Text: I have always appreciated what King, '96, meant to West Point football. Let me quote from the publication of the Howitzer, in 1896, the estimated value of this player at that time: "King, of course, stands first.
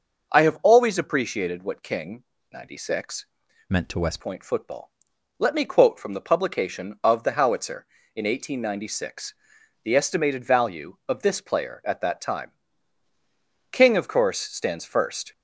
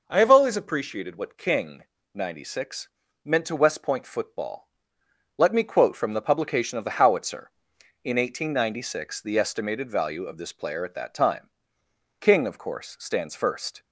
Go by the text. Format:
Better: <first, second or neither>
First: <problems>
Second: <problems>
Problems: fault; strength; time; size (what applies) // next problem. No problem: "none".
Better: second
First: starts louder than the rest; noticeable; until 1.3 s; 6 dB // changes voice from "meant" to "West"; from 3.6 to 4.1 s; 0.5 s long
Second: none